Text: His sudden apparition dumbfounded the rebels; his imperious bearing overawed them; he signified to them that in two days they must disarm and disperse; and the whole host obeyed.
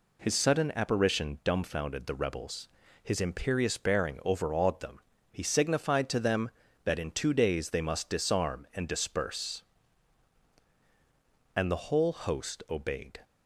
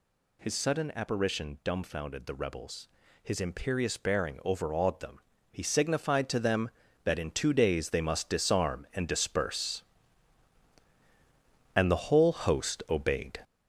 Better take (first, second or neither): first